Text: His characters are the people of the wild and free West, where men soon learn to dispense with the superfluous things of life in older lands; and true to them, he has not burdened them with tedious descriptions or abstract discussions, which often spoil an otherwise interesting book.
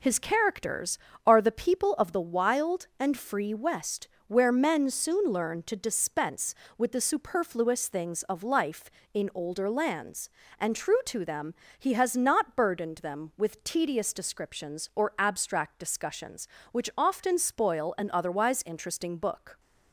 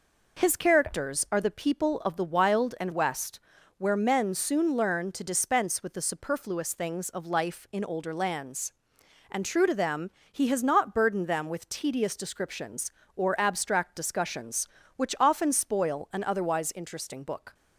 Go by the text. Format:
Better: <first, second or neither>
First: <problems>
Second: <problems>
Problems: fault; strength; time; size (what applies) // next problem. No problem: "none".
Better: first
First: none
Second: skips "free"; at 2.9 s